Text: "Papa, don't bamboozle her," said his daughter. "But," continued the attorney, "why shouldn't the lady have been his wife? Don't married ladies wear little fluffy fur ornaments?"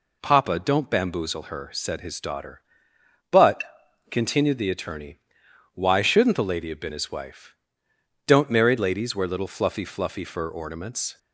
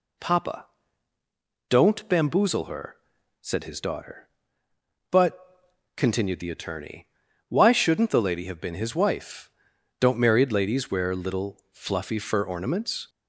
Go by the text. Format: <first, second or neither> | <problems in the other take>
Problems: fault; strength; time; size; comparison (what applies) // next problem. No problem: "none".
second | says "fluffy" twice; at 9.8 s